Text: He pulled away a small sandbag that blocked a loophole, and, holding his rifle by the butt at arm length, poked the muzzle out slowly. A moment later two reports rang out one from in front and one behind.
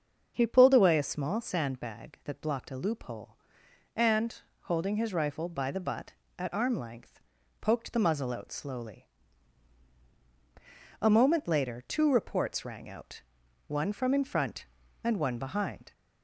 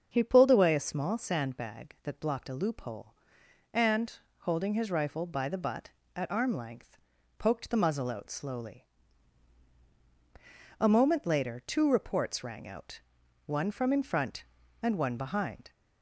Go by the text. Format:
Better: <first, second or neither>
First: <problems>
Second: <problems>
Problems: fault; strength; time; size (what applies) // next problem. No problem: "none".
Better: neither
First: starts louder than the rest; until 1.3 s; 6.5 dB // pauses between "out" and "one"; noticeable; at 13.2 s; 0.46 s long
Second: starts louder than the rest; until 1.1 s; 6.5 dB // pauses between "out" and "one"; noticeable; at 12.9 s; 0.46 s long